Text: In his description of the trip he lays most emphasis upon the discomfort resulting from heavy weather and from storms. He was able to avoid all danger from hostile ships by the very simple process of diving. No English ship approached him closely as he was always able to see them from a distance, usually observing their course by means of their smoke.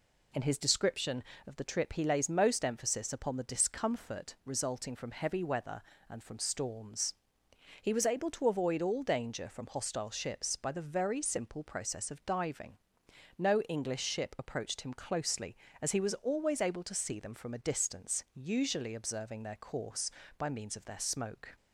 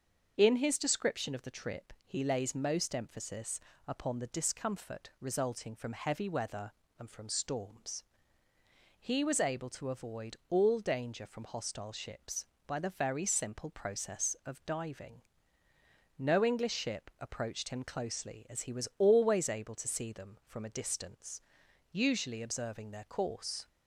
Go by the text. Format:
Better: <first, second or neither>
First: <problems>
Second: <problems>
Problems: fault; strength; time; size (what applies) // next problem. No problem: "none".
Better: first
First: none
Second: starts louder than the rest; until 1.3 s; 6.5 dB // pauses between "emphasis" and "upon"; slight; at 3.5 s; 0.28 s long // stops before "by means of their smoke"; at 23.6 s